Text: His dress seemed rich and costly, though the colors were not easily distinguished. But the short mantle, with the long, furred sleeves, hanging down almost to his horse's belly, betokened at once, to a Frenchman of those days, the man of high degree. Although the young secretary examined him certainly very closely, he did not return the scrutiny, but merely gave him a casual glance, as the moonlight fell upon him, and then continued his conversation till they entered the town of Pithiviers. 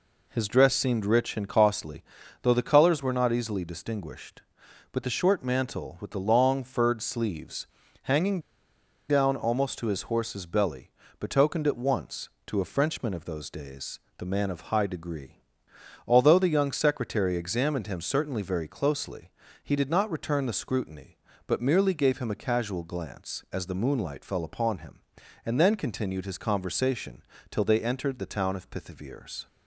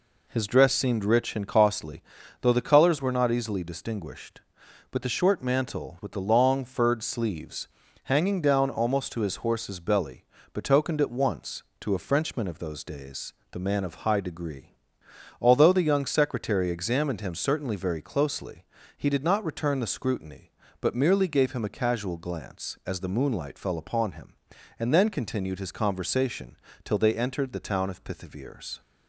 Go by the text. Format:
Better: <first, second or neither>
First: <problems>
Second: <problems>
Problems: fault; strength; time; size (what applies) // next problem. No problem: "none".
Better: second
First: pauses between "hanging" and "down"; noticeable; at 8.3 s; 0.69 s long // pauses between "conversation" and "till"; slight; at 27.2 s; 0.28 s long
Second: pauses between "conversation" and "till"; slight; at 26.5 s; 0.28 s long